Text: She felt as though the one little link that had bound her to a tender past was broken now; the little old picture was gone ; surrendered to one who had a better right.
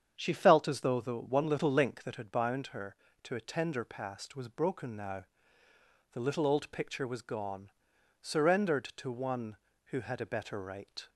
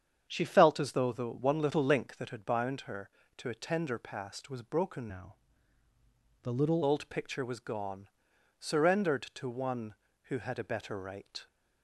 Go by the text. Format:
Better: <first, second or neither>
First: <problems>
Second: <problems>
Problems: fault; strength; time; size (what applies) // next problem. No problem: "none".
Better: first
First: starts louder than the rest; strong; until 1.1 s; 8 dB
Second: starts louder than the rest; strong; until 1.3 s; 8 dB // changes voice from "now" to "little"; from 5.0 to 6.8 s; 1.8 s long